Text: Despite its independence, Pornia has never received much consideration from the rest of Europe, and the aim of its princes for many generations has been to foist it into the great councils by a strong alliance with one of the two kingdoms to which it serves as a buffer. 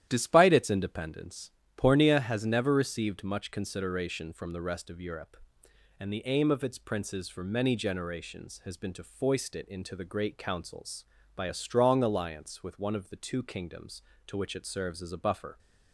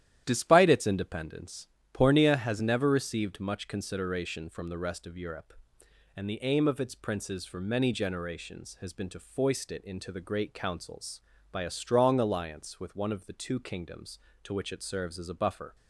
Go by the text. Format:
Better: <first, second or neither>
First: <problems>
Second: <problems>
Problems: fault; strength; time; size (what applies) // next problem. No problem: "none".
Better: neither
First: starts louder than the rest; strong; until 1.1 s; 11.5 dB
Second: starts louder than the rest; strong; until 1.2 s; 11.5 dB